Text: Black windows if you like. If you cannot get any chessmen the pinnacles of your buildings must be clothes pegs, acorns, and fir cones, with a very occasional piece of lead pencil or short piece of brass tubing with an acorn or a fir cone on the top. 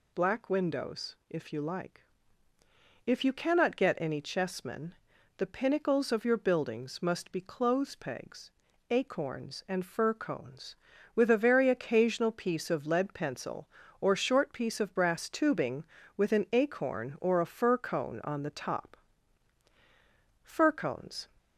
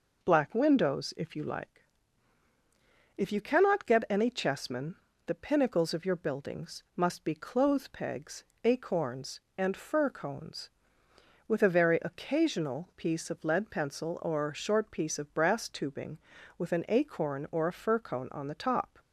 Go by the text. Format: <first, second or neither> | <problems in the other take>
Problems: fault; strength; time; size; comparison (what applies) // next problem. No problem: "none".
second | pauses between "chessmen" and "the"; at 4.9 s; 0.44 s long; slight in the second // goes on to say "Fir cones"; noticeable; from 20.4 s on; 0.84 s long